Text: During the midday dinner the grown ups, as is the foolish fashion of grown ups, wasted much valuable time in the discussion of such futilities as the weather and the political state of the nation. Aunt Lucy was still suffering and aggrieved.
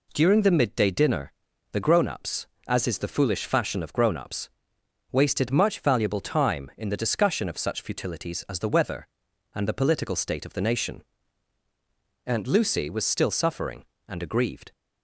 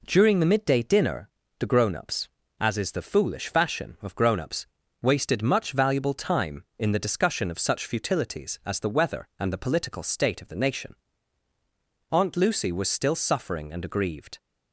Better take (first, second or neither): neither